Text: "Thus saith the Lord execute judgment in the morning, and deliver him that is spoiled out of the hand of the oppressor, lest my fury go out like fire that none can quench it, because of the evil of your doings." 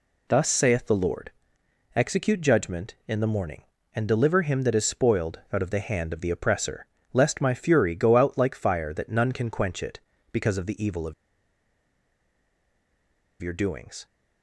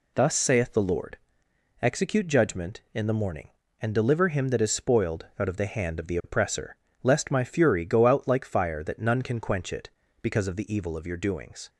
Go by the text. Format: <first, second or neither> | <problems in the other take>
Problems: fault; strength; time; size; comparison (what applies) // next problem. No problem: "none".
second | pauses between "Lord" and "execute"; noticeable; at 1.3 s; 0.64 s long; noticeable in the second // pauses between "of" and "your"; strong; at 11.1 s; 2.2 s long